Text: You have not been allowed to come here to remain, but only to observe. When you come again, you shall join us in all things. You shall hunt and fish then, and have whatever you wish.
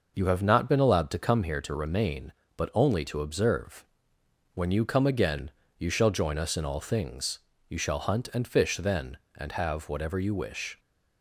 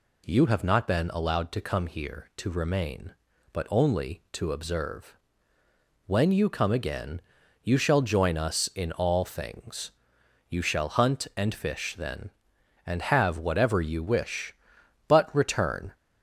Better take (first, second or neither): first